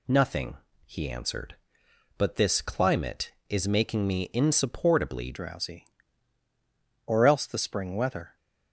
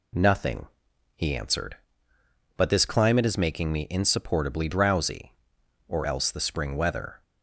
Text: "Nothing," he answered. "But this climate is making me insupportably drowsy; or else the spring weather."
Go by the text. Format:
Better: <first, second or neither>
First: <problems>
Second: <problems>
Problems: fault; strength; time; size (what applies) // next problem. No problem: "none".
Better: second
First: changes voice at "drowsy"; from 5.3 s on; 3.0 s long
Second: none